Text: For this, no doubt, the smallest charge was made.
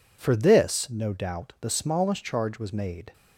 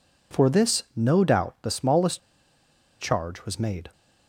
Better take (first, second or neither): first